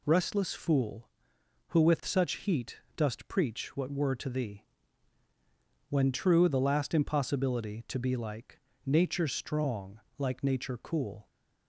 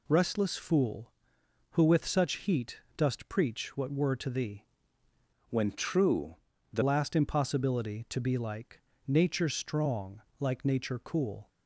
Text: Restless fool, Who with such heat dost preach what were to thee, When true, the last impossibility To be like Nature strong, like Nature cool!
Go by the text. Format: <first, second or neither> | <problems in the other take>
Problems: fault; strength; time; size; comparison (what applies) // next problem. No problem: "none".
first | pauses between "heat" and "dost"; slight; at 2.7 s; 0.16 s long; slight in the first // changes voice from "When" to "the"; from 5.4 to 6.8 s; 1.4 s long // pauses between "like" and "Nature"; slight; at 8.8 s; 0.26 s long; slight in the first